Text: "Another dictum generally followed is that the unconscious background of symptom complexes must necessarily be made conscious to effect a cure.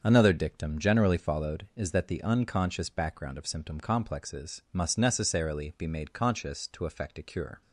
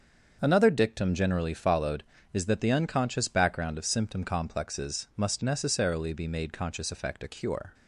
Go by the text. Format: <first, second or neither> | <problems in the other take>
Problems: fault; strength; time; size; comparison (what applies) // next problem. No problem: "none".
first | starts louder than the rest; until 1.4 s; 7 dB; also in the first // skips "to"; at 6.9 s